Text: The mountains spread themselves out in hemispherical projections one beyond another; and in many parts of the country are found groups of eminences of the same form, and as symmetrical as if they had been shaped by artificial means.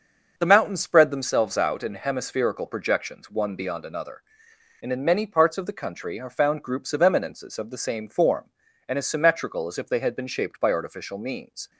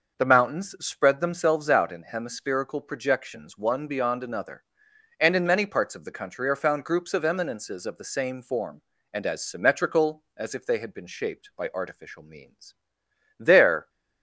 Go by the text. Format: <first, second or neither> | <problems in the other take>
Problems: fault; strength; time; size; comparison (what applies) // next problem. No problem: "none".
first | goes on to say "There"; slight; from 13.4 s on; 0.48 s long